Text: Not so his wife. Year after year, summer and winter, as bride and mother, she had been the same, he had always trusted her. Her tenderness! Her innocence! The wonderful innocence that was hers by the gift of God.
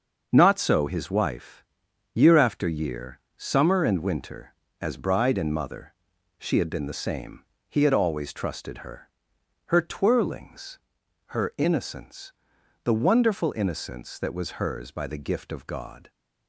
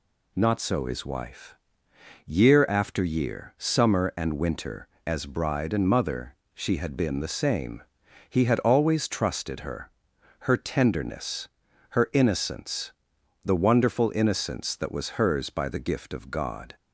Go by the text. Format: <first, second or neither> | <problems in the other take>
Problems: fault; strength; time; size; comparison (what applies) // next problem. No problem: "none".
second | starts louder than the rest; until 1.3 s; 6.5 dB // says "twirlings" for "tenderness"; at 9.8 s